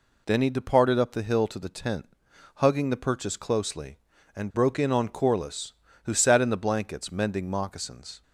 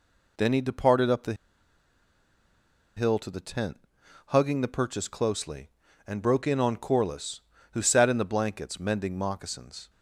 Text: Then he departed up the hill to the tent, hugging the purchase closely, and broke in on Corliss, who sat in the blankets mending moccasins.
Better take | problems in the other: first | pauses between "the" and "hill"; strong; at 1.3 s; 1.6 s long

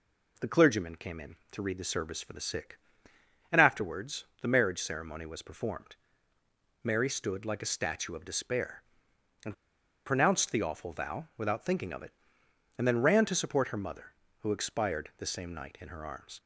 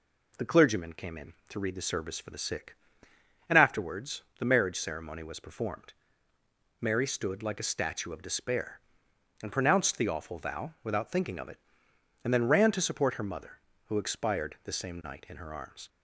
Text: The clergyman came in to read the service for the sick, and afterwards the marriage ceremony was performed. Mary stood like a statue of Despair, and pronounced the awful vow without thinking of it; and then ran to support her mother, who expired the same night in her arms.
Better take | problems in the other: second | pauses between "afterwards" and "the"; slight; at 4.2 s; 0.16 s long; slight in the second // pauses between "and" and "pronounced"; noticeable; at 9.5 s; 0.51 s long

